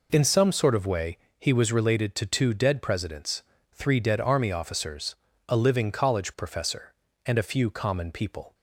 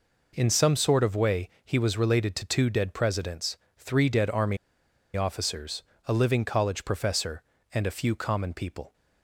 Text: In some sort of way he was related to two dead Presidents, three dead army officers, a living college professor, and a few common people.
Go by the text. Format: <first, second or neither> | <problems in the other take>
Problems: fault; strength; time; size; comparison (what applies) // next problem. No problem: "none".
first | pauses between "way" and "he"; slight; at 1.4 s; 0.16 s long; slight in the first // pauses between "army" and "officers"; noticeable; at 4.5 s; 0.59 s long